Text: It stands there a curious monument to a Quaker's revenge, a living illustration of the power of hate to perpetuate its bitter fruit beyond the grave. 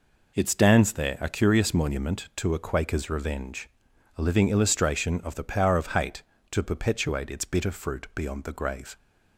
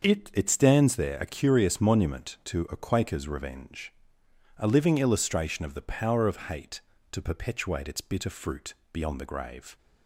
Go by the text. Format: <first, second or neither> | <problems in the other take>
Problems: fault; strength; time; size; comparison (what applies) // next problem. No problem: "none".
first | starts louder than the rest; until 1.0 s; 6.5 dB // says "It" twice; at 0.3 s // pauses between "fruit" and "beyond"; slight; at 8.7 s; 0.18 s long